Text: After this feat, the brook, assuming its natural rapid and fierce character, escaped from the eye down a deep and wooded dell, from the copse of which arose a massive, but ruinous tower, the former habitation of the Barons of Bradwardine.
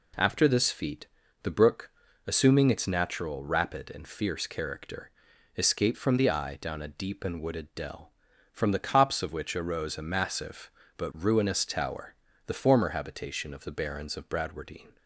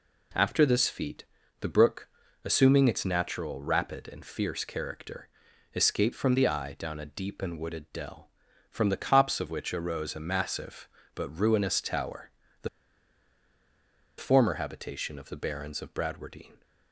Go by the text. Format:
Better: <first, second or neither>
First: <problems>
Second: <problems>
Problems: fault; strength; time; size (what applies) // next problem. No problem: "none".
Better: first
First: none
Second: pauses between "the" and "former"; strong; at 12.6 s; 1.5 s long